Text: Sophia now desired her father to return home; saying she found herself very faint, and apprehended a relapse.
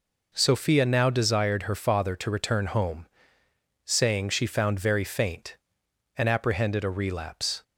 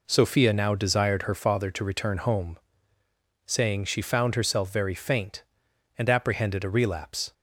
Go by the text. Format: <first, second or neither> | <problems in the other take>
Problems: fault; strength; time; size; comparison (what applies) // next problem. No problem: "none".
second | skips "herself"; at 4.7 s